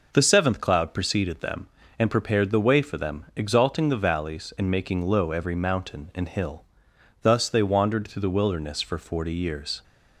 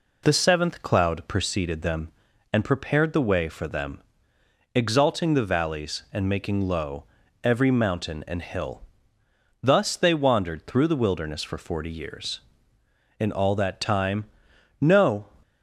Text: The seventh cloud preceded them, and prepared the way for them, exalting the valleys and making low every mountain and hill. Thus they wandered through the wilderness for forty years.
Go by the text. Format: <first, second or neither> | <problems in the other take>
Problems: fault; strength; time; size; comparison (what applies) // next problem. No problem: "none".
first | pauses between "low" and "every"; at 7.0 s; 0.38 s long // goes on to say "In all that time no"; strong; from 13.2 s on; 2.0 s long